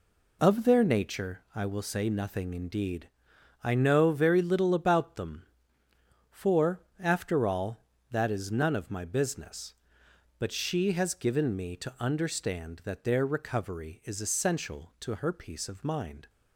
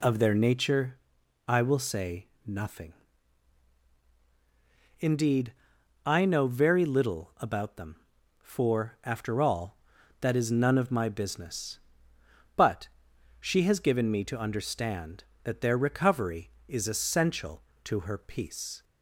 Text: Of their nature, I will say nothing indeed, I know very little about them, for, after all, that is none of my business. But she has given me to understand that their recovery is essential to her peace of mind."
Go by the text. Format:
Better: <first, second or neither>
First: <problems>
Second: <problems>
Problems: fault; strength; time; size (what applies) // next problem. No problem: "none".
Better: first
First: none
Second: pauses between "say" and "nothing"; slight; at 2.2 s; 0.18 s long // pauses between "nothing" and "indeed"; strong; at 2.9 s; 2.0 s long // pauses between "But" and "she"; noticeable; at 12.8 s; 0.52 s long // stops before "of mind"; at 18.8 s